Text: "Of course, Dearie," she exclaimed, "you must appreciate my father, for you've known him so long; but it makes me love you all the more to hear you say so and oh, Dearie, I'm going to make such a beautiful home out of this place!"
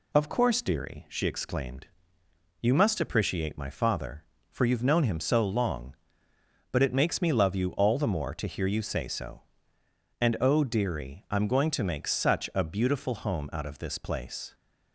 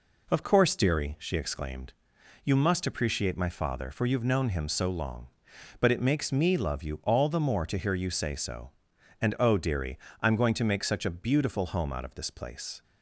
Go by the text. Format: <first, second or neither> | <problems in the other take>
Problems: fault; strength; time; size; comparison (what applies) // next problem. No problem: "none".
neither | none